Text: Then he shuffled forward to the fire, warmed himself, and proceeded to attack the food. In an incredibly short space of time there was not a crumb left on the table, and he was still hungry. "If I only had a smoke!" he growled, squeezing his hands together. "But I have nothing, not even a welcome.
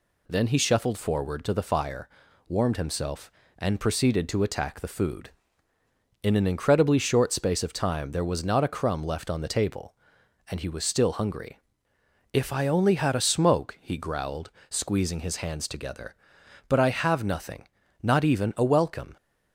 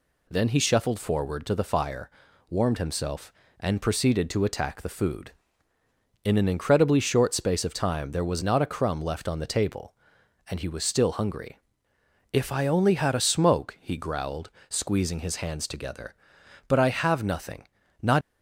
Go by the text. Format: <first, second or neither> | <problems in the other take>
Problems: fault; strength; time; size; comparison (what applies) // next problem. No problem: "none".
first | stops before "even a welcome"; at 18.2 s